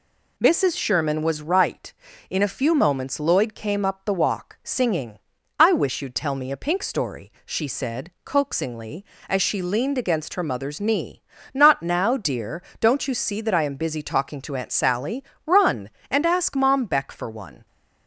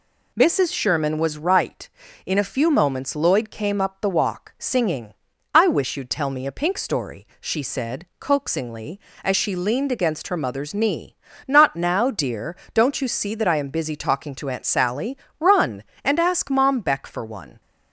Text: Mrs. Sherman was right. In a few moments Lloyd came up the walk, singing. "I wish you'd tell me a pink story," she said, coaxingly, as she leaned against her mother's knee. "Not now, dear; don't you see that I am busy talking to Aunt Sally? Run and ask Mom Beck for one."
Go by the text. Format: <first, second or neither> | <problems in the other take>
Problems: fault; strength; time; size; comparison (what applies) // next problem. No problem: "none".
neither | none